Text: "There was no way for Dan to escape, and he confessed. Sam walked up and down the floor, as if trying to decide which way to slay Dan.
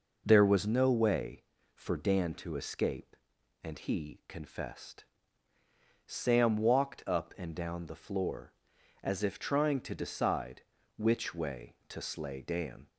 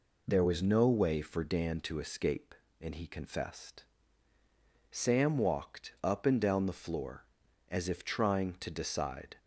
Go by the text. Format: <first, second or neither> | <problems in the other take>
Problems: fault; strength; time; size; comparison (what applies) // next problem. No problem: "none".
first | stops before "which way to slay Dan"; at 9.3 s